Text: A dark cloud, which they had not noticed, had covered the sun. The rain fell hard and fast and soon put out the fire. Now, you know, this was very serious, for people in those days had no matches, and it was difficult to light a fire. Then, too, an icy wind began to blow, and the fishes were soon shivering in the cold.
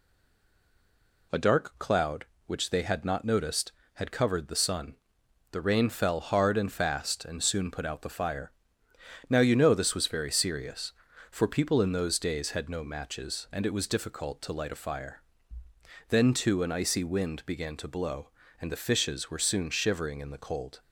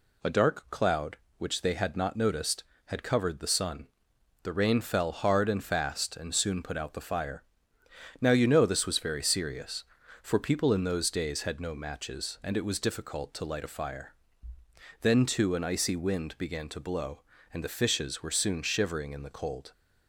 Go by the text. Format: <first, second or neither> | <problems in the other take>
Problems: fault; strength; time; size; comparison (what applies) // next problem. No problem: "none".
second | stays silent before the first word; noticeable; until 1.3 s; 1.3 s long